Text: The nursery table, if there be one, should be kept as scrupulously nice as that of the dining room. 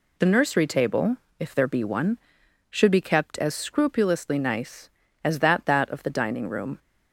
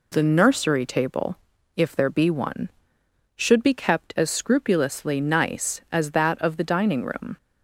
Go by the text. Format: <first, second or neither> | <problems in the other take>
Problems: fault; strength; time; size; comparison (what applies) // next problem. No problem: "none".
second | says "that" twice; at 5.6 s